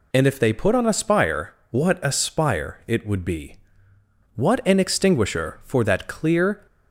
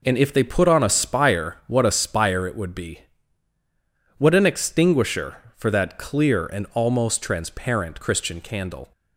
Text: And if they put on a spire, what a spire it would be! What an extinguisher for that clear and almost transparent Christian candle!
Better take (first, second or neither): second